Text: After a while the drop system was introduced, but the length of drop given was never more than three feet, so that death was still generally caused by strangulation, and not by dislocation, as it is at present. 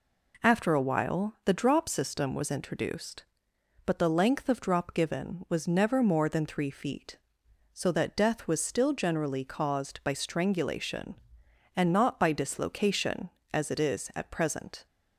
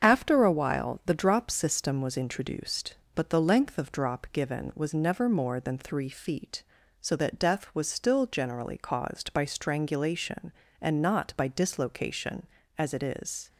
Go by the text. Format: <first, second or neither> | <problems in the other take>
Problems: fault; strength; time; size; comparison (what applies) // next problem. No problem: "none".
first | starts louder than the rest; until 1.1 s; 7 dB // stops before "at present"; at 13.4 s